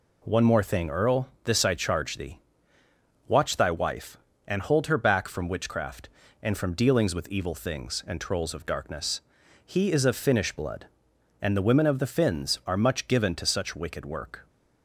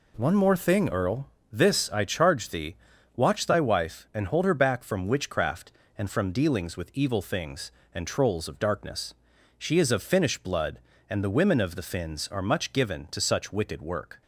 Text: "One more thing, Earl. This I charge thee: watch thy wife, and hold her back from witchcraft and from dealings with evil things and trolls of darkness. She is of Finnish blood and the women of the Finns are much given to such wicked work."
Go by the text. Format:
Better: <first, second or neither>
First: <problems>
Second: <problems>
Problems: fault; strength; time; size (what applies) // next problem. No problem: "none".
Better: second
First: says "He" for "She"; at 9.6 s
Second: none